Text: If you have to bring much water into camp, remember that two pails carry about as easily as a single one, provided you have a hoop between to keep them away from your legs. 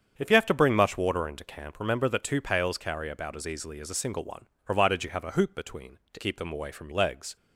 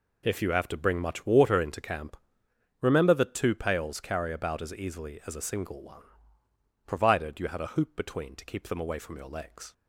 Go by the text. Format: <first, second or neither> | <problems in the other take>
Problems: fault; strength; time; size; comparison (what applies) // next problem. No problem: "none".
second | starts louder than the rest; strong; until 1.1 s; 7.5 dB // skips "your"; at 6.9 s